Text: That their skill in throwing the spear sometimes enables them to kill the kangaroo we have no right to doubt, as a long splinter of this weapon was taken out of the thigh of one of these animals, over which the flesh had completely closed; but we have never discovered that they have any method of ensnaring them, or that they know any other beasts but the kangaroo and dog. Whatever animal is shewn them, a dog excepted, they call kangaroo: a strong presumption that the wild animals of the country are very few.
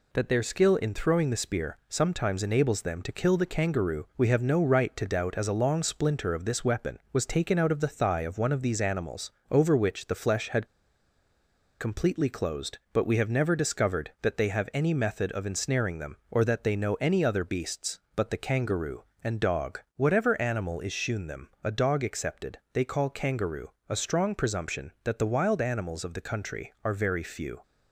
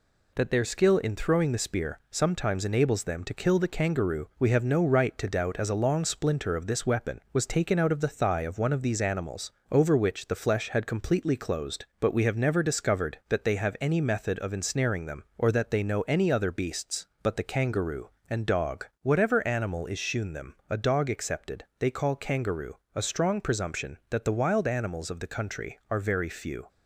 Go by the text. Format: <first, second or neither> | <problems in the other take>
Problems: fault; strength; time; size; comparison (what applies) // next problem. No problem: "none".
second | pauses between "had" and "completely"; at 10.6 s; 1.1 s long